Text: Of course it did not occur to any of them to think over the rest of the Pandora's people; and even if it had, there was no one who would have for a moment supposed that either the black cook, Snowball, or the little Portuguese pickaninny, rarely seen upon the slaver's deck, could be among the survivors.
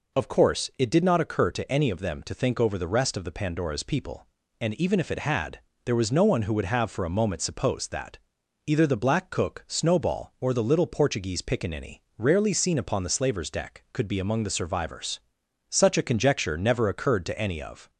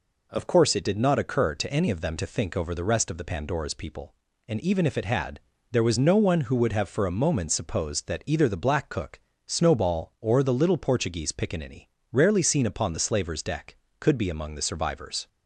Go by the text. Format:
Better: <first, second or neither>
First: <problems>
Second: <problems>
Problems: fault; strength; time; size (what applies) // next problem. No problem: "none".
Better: second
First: pauses between "that" and "either"; noticeable; at 8.1 s; 0.48 s long // goes on to say "Such a conjecture never occurred to any of"; strong; from 15.6 s on; 2.2 s long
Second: none